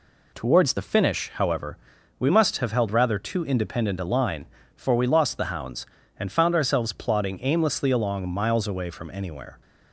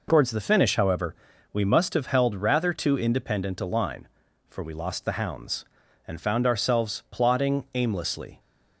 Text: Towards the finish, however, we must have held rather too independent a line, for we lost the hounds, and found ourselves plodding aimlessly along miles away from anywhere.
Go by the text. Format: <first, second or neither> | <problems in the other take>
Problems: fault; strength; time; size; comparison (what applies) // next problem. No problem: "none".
first | stops before "along miles away from anywhere"; at 8.3 s